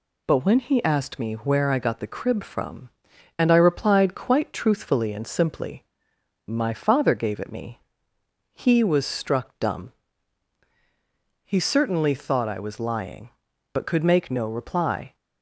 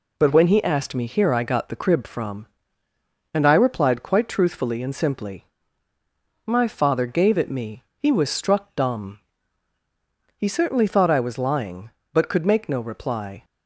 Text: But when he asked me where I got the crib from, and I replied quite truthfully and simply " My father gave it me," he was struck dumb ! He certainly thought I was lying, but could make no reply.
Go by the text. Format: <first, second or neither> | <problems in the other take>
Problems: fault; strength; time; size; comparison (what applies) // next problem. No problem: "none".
first | says "here" for "where"; at 1.0 s